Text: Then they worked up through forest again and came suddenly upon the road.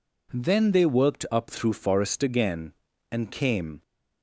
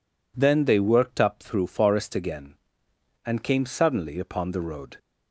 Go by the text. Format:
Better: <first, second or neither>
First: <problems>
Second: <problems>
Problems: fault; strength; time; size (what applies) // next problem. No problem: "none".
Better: second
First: stops before "suddenly upon the road"; at 3.8 s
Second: none